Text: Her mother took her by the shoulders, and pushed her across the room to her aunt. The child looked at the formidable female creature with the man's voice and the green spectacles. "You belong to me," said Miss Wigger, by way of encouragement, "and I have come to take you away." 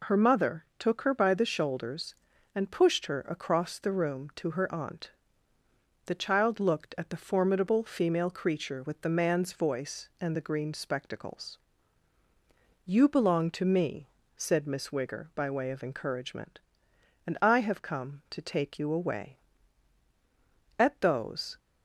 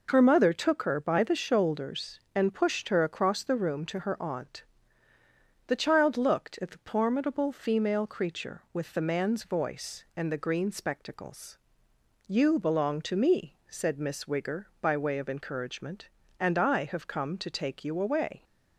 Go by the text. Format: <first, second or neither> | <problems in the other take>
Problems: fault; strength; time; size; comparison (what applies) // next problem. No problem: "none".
second | goes on to say "At those"; noticeable; from 20.7 s on; 0.80 s long